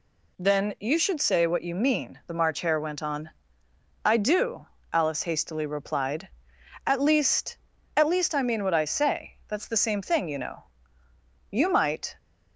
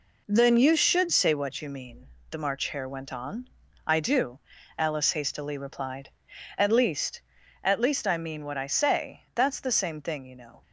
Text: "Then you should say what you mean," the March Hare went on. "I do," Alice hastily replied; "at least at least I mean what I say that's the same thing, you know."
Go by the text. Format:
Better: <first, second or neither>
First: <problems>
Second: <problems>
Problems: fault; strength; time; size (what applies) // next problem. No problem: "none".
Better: second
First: goes on to say "You might"; noticeable; from 11.5 s on; 0.66 s long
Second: none